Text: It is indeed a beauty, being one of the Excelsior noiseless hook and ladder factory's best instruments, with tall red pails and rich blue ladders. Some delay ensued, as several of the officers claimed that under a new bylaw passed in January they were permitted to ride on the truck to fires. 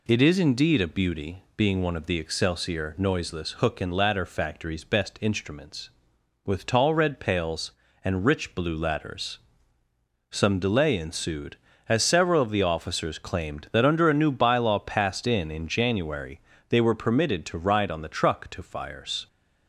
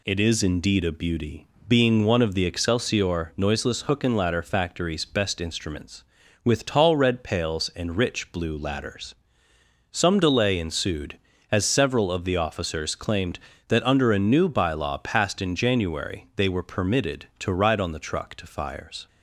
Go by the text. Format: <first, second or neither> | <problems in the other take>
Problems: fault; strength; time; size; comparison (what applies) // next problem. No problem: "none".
second | says "in" twice; at 15.5 s // pauses between "January" and "they"; slight; at 16.3 s; 0.30 s long